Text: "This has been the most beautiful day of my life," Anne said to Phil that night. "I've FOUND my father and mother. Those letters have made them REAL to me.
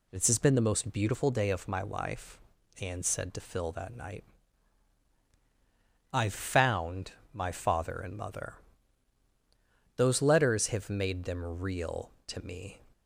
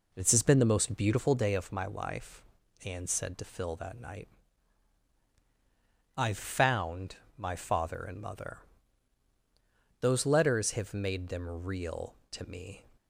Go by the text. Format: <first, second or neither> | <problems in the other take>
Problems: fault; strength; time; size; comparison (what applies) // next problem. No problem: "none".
first | starts louder than the rest; until 1.7 s; 4 dB // pauses between "FOUND" and "my"; slight; at 7.1 s; 0.18 s long; slight in the first